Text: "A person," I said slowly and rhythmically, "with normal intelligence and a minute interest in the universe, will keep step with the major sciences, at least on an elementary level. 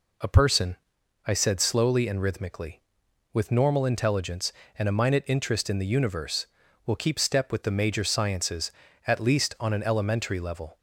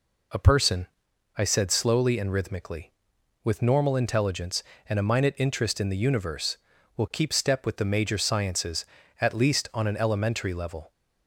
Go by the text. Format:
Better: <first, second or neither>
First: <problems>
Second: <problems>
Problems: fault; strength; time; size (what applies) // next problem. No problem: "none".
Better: neither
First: none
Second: none